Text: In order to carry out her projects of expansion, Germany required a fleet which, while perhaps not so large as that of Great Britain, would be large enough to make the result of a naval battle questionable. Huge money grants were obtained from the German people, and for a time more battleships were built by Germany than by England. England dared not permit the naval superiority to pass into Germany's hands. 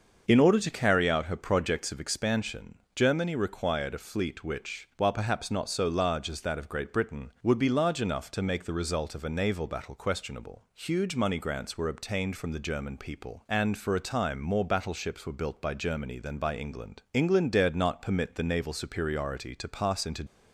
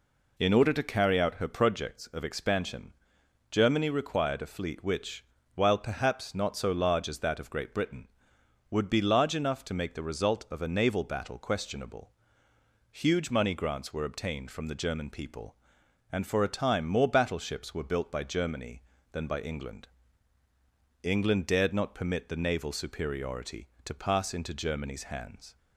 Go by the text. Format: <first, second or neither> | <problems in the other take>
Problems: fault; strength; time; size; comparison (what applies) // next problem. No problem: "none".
second | starts louder than the rest; until 1.2 s; 6.5 dB // stops before "Germany's hands"; at 20.2 s